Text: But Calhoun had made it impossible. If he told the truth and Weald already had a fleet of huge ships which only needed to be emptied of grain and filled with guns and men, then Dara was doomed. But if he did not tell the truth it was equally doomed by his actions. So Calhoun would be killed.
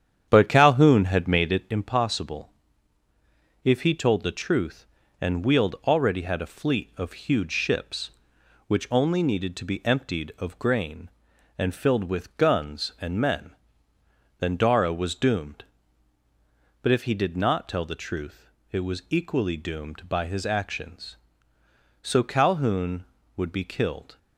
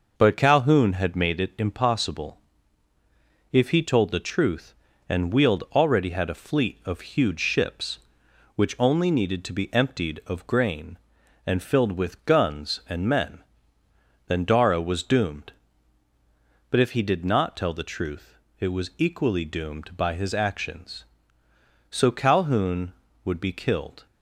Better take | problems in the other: second | starts louder than the rest; strong; until 1.7 s; 9 dB // pauses between "truth" and "it"; slight; at 18.4 s; 0.22 s long; slight in the second

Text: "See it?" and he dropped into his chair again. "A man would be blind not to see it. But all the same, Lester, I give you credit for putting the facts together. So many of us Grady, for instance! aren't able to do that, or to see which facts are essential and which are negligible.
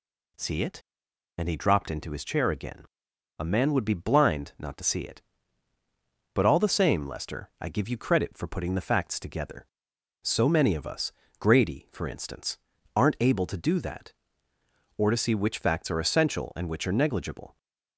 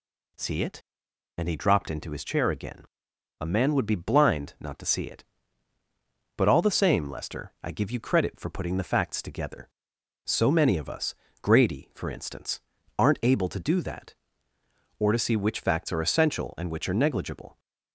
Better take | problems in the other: neither | pauses between "us" and "Grady"; slight; the same in both

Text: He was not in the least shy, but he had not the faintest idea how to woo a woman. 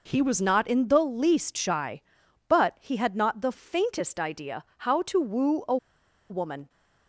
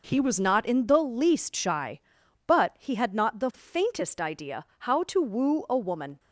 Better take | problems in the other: second | pauses between "idea" and "how"; slight; at 4.6 s; 0.24 s long; slight in the second // pauses between "a" and "woman"; noticeable; at 5.7 s; 0.53 s long

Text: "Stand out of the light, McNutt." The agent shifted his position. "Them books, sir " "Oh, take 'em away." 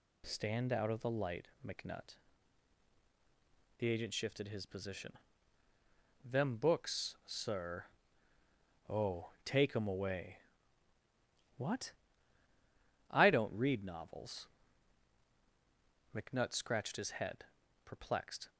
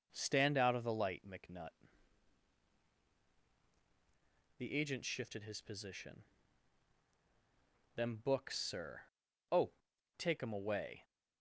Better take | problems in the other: second | goes on to say "What I don't read novels McNutt scratched his head perplexed"; strong; from 11.5 s on; 6.9 s long

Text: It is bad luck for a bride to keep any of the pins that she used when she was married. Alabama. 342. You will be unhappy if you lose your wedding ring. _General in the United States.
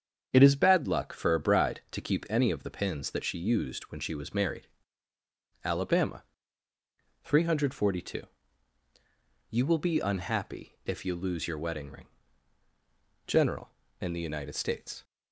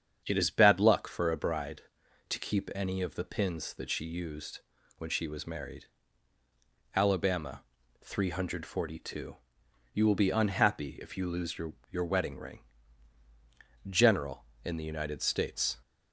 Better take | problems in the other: first | starts louder than the rest; strong; until 1.2 s; 8 dB; strong in the first // pauses between "used" and "when"; slight; at 4.6 s; 0.36 s long // says "your" twice; at 11.8 s

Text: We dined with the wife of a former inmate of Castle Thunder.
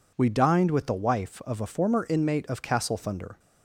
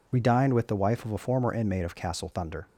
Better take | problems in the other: neither | none

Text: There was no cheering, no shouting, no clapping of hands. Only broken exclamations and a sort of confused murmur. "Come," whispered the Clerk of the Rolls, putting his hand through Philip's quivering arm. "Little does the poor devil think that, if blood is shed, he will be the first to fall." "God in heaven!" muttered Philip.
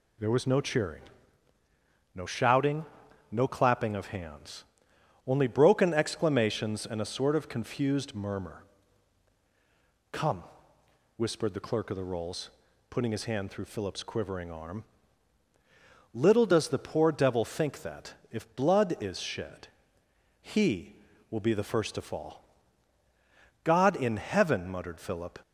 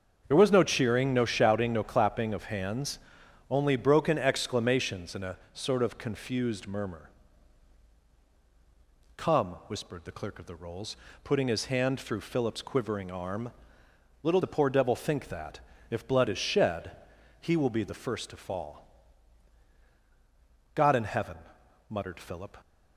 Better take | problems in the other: first | starts louder than the rest; until 1.2 s; 6.5 dB // pauses between "a" and "sort"; slight; at 5.3 s; 0.16 s long // skips "does"; at 14.4 s

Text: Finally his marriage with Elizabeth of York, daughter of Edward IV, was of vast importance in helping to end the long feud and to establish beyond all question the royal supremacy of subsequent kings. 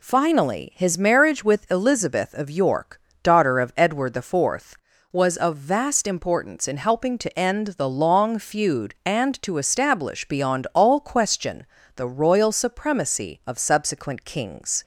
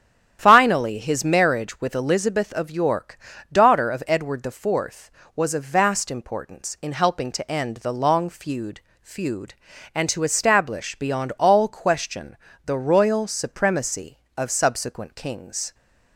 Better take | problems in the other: first | starts louder than the rest; strong; until 1.4 s; 9.5 dB // says "feud" twice; at 9.0 s // pauses between "question" and "the"; slight; at 12.3 s; 0.26 s long; slight in the first

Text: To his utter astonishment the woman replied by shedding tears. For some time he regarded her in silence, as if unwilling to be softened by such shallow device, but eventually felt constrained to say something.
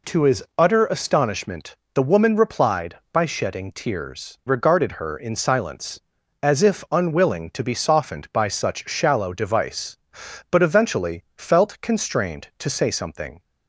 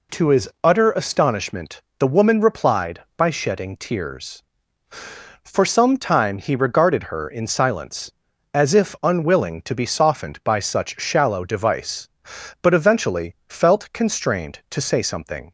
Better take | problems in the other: second | pauses between "astonishment" and "the"; slight; at 1.7 s; 0.18 s long; slight in the second // skips "For some time he"; at 4.4 s

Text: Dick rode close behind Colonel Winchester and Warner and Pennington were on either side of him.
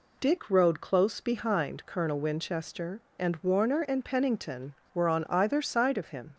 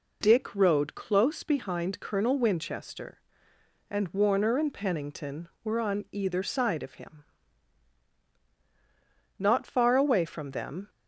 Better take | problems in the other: first | goes on to say "Not far away from them"; from 9.4 s on; 1.4 s long

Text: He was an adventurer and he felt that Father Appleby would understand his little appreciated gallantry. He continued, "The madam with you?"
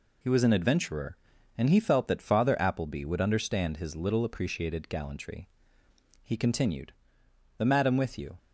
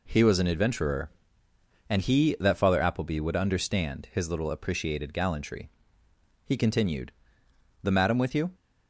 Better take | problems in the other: first | skips "felt"; at 2.3 s

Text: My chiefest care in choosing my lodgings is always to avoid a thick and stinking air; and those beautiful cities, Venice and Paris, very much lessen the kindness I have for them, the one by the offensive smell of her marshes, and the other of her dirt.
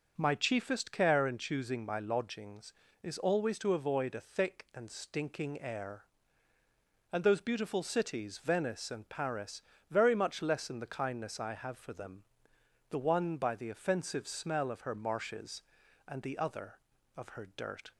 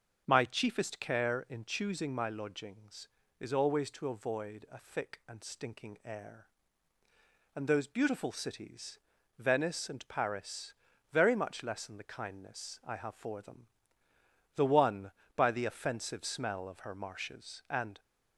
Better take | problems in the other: first | starts louder than the rest; until 1.2 s; 7 dB; also in the first // stops before "the other of her dirt"; at 17.9 s

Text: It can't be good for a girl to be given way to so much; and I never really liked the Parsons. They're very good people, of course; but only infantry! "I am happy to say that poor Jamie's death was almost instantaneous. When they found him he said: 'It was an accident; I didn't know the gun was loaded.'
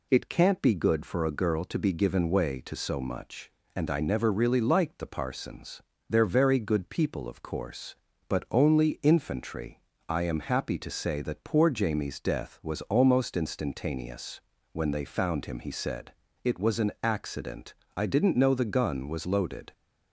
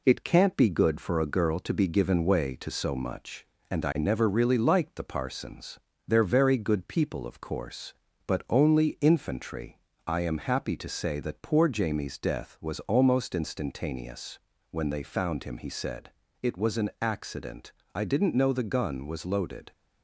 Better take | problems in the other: first | gets quieter; slight; throughout; 2.5 dB

